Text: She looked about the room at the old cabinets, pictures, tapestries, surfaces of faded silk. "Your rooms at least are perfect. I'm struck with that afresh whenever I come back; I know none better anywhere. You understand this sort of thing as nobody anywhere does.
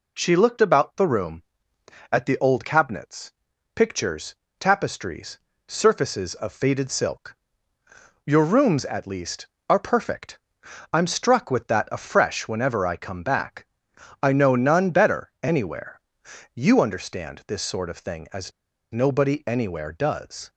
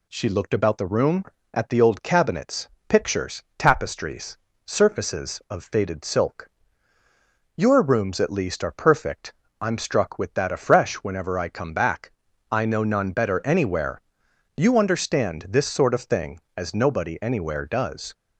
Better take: second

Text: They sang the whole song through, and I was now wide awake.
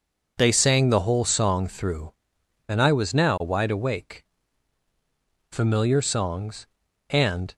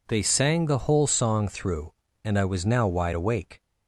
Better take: second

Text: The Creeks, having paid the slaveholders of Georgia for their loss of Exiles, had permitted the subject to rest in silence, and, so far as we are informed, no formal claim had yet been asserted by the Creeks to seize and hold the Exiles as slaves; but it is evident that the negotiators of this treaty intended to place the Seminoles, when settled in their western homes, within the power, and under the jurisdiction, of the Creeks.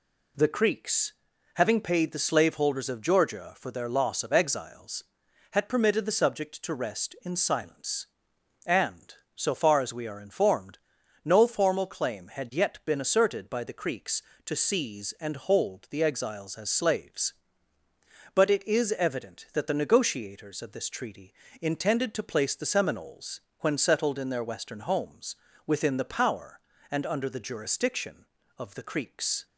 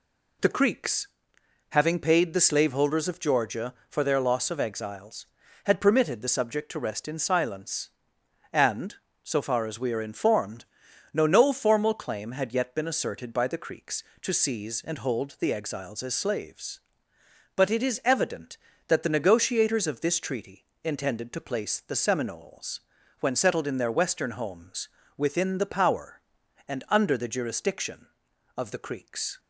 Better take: first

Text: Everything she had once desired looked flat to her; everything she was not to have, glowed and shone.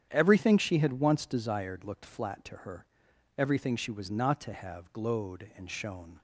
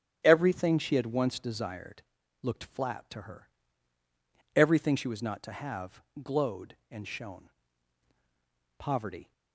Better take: first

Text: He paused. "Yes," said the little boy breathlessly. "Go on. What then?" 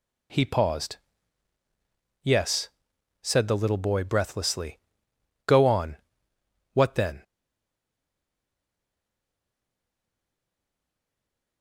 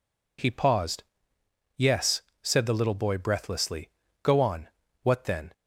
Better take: second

